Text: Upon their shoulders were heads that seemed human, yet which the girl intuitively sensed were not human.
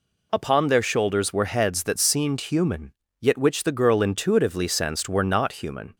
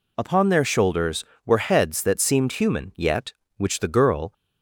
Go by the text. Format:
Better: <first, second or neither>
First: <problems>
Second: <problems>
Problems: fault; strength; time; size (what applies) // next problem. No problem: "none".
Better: first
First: none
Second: stops before "intuitively sensed were not human"; at 4.3 s